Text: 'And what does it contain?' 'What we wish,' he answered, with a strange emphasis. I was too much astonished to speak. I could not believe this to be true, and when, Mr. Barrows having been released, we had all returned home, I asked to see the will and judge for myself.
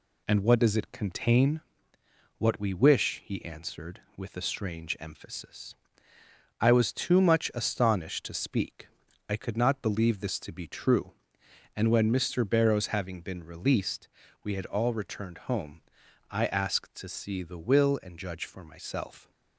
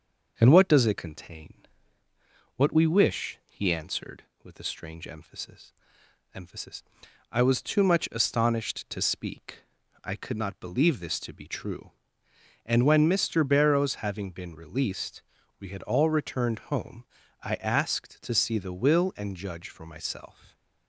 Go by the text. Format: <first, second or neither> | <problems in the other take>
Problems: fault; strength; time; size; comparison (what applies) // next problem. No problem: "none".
first | says "emphasis" twice; at 6.3 s